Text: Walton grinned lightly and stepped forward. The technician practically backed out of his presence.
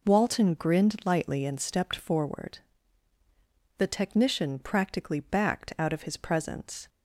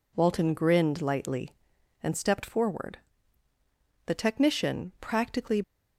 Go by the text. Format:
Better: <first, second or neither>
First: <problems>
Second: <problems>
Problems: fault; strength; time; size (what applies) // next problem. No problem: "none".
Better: first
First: none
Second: stops before "backed out of his presence"; at 5.6 s